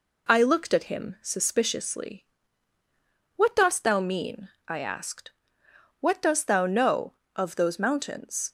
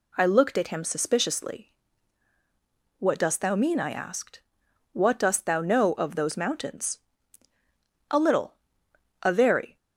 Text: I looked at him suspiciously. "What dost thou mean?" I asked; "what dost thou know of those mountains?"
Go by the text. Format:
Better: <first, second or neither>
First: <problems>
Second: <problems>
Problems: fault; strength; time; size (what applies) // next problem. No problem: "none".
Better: first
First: none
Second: goes on to say "A little a very"; strong; from 8.0 s on; 1.6 s long